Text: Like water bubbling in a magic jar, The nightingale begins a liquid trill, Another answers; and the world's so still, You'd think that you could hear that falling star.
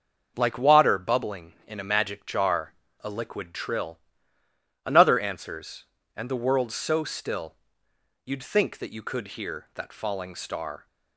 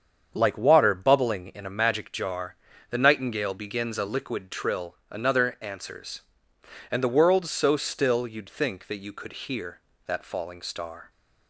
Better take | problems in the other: second | starts louder than the rest; until 1.3 s; 6.5 dB; strong in the second // skips "The nightingale begins"; at 2.8 s

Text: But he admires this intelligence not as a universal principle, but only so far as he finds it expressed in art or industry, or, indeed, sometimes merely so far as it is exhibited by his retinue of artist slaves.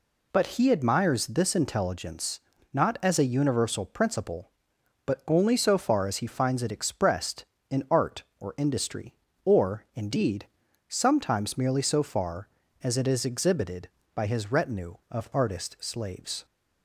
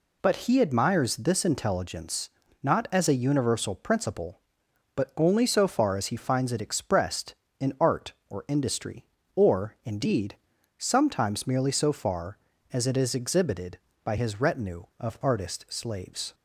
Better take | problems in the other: neither | pauses between "intelligence" and "not"; slight; the same in both

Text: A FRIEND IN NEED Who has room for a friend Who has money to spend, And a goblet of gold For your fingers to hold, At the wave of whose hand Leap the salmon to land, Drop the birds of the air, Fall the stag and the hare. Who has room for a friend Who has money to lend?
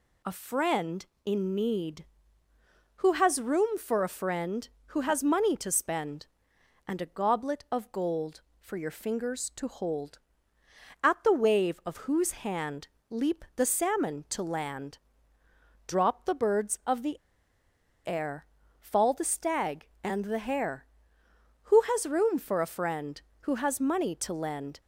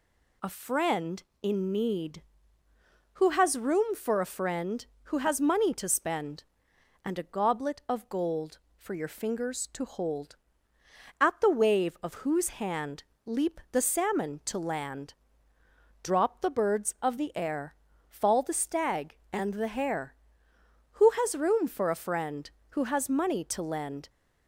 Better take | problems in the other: second | pauses between "hand" and "Leap"; slight; at 12.8 s; 0.20 s long; slight in the second // pauses between "the" and "air"; noticeable; at 17.1 s; 0.89 s long

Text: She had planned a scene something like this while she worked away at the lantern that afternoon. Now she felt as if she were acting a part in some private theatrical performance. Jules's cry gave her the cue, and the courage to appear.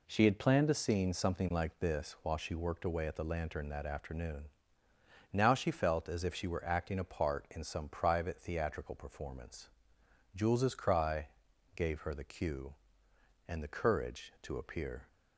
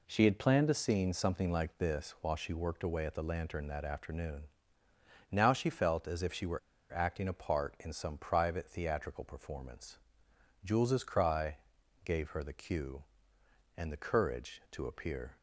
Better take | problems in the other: first | pauses between "were" and "acting"; slight; at 6.5 s; 0.32 s long // pauses between "cry" and "gave"; noticeable; at 11.5 s; 0.48 s long; noticeable in the first

